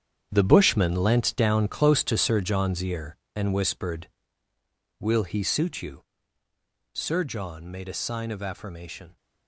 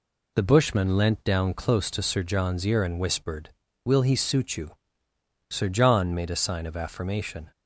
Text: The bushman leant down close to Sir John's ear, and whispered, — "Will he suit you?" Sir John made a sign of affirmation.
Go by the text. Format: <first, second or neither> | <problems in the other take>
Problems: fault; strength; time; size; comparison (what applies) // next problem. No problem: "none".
second | gets quieter; strong; throughout; 11.5 dB